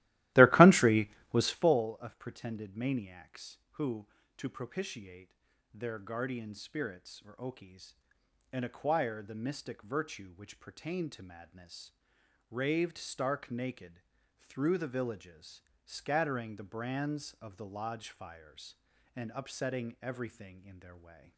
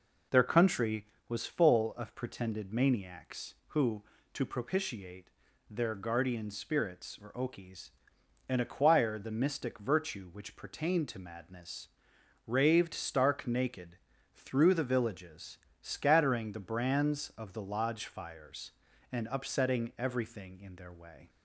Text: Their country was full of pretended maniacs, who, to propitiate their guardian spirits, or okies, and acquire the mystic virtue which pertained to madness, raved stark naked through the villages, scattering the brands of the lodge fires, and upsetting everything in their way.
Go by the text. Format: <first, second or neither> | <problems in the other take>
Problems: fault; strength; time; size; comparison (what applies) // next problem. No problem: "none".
second | starts louder than the rest; strong; until 1.8 s; 16 dB // pauses between "propitiate" and "their"; at 5.3 s; 0.40 s long; also in the second // pauses between "naked" and "through"; at 14.0 s; 0.38 s long; also in the second